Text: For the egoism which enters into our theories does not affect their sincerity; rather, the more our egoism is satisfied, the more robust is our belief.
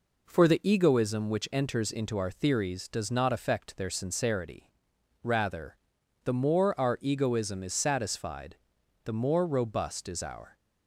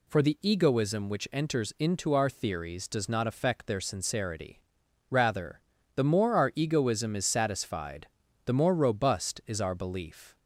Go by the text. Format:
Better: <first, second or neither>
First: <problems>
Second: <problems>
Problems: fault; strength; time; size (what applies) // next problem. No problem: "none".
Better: second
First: stops before "belief"; at 10.5 s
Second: none